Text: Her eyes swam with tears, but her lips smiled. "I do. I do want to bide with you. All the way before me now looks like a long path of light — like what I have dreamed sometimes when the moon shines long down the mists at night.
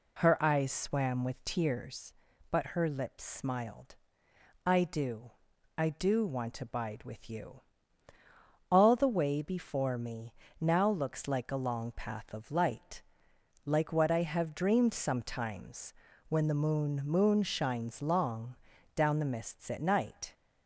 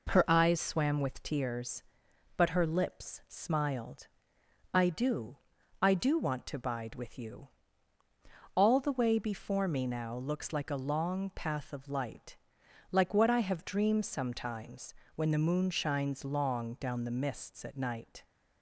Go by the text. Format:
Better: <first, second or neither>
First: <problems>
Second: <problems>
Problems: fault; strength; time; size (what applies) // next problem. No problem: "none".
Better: second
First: pauses between "me" and "now"; slight; at 10.3 s; 0.26 s long // pauses between "sometimes" and "when"; slight; at 15.9 s; 0.36 s long // says "moon" twice; at 17.0 s // pauses between "long" and "down"; at 18.5 s; 0.40 s long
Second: pauses between "sometimes" and "when"; slight; at 14.9 s; 0.22 s long